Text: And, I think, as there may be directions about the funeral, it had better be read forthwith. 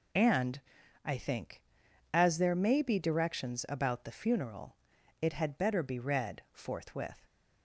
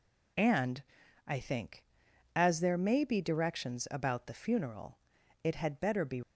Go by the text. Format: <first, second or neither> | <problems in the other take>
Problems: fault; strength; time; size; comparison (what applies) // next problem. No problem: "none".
first | stops before "read forthwith"; at 6.2 s